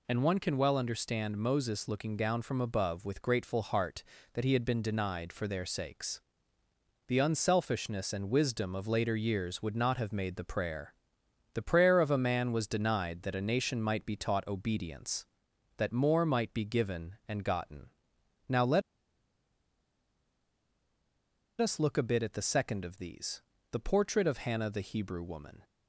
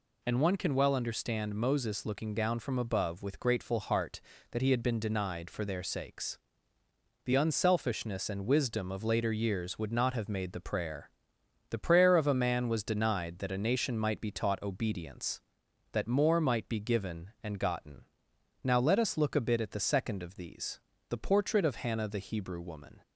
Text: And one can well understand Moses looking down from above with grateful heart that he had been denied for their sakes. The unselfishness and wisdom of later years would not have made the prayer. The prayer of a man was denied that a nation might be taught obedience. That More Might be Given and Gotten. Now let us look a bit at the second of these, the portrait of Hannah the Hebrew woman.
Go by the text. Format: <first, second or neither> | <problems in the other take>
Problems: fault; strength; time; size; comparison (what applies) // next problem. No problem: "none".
second | pauses between "let" and "us"; strong; at 18.8 s; 2.8 s long